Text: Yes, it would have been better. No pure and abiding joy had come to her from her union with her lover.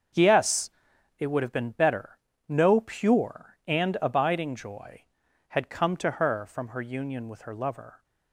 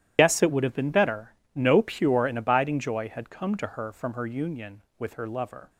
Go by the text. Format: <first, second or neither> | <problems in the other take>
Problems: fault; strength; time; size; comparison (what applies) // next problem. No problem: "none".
first | loses the start of "Yes"; at 0.1 s; 80 ms // starts louder than the rest; strong; until 1.1 s; 12 dB; also in the first